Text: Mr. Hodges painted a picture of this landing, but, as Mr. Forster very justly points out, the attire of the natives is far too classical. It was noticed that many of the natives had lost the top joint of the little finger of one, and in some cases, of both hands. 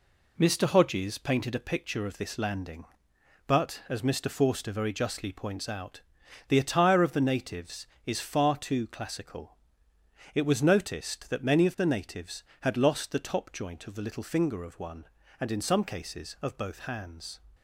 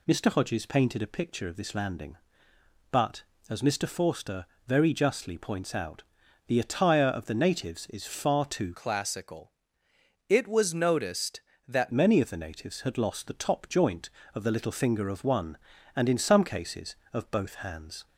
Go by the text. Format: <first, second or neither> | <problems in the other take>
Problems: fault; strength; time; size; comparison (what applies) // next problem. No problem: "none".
first | pauses between "Forster" and "very"; slight; at 4.4 s; 0.20 s long // changes voice from "classical" to "that"; from 8.7 to 11.9 s; 3.2 s long